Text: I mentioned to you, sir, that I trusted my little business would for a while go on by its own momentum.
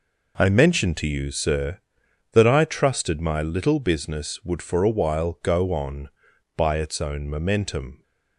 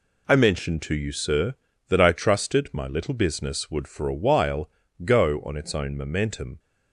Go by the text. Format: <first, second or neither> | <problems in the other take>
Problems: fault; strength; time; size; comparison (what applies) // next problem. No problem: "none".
first | pauses between "while" and "go"; slight; at 4.7 s; 0.32 s long // skips "by"; at 5.5 s